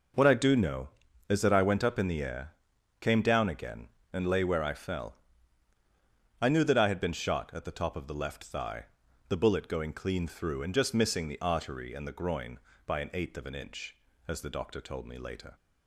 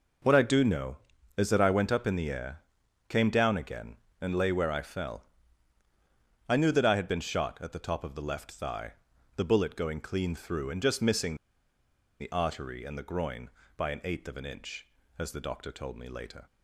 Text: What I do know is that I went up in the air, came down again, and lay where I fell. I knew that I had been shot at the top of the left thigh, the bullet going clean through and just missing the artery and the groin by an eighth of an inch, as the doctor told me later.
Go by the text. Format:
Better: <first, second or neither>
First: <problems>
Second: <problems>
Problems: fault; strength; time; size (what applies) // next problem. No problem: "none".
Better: first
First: none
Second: pauses between "missing" and "the"; noticeable; at 11.3 s; 0.85 s long